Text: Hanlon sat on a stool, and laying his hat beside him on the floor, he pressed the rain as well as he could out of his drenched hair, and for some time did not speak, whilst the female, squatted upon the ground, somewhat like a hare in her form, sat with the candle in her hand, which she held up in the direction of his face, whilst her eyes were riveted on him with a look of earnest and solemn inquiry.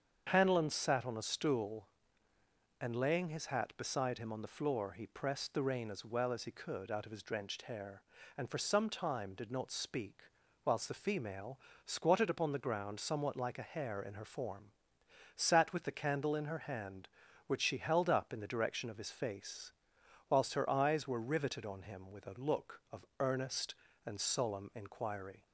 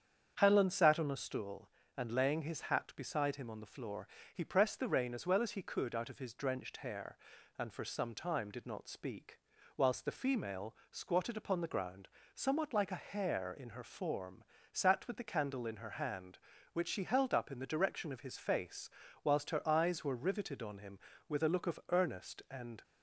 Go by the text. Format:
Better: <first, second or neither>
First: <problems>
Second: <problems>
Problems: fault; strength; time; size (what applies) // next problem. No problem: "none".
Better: first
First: starts louder than the rest; strong; until 1.3 s; 7 dB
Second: starts louder than the rest; strong; until 1.3 s; 8 dB // stops before "solemn inquiry"; at 22.8 s